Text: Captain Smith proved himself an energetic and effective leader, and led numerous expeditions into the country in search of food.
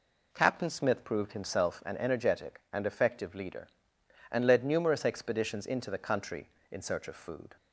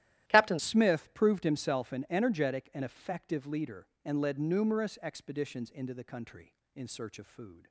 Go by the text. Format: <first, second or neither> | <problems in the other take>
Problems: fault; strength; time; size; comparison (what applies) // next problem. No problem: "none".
first | starts louder than the rest; strong; until 1.3 s; 13 dB // changes voice at "Smith"; from 0.5 s on; 7.1 s long